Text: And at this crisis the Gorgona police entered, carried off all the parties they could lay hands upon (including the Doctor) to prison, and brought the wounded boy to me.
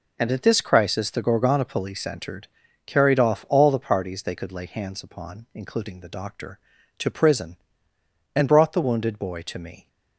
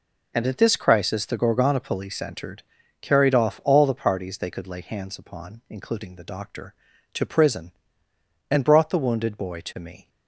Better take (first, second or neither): neither